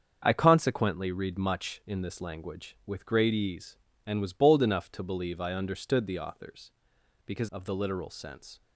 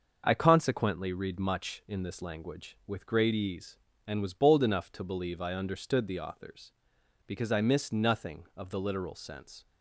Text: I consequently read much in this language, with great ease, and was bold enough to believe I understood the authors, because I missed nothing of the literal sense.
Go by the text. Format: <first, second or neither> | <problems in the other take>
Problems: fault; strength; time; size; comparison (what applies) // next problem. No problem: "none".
second | starts louder than the rest; strong; until 1.2 s; 7 dB; also in the second // skips "I missed nothing"; at 7.4 s